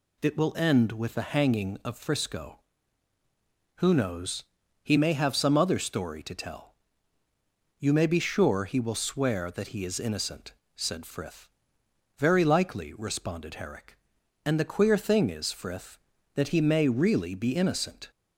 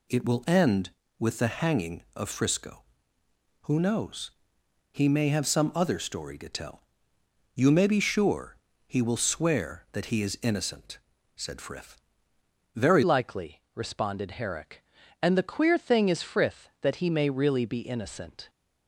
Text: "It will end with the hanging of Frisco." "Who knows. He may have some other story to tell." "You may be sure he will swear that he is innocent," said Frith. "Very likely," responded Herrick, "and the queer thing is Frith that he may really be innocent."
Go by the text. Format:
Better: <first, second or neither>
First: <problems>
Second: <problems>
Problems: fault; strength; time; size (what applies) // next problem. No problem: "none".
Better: first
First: none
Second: pauses between "sure" and "he"; slight; at 8.5 s; 0.30 s long // changes voice at "likely"; from 13.0 s on; 5.4 s long